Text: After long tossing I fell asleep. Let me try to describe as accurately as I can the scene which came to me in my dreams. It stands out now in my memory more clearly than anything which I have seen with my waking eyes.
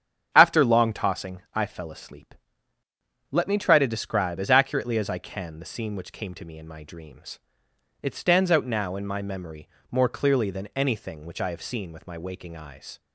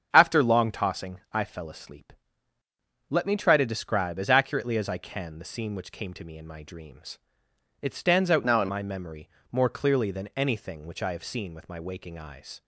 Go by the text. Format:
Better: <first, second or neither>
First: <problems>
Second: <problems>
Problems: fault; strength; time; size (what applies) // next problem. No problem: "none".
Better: first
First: starts louder than the rest; strong; until 1.3 s; 8 dB // pauses between "memory" and "more"; slight; at 9.6 s; 0.22 s long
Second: starts louder than the rest; strong; until 1.1 s; 7.5 dB // changes voice from "now" to "in"; from 8.4 to 8.6 s; 0.2 s long // pauses between "memory" and "more"; slight; at 9.2 s; 0.22 s long